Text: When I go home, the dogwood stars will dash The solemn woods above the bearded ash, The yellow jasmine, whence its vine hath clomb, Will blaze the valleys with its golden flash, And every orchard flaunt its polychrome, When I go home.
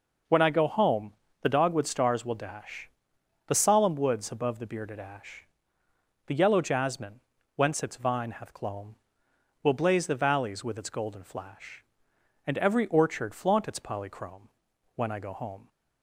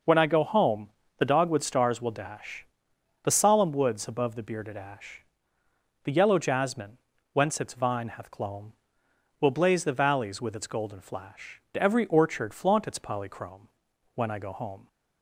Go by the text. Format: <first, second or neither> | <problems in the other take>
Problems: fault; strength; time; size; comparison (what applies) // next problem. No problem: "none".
first | pauses between "dash" and "The"; noticeable; at 2.6 s; 0.58 s long; noticeable in the first // skips "And"; at 11.6 s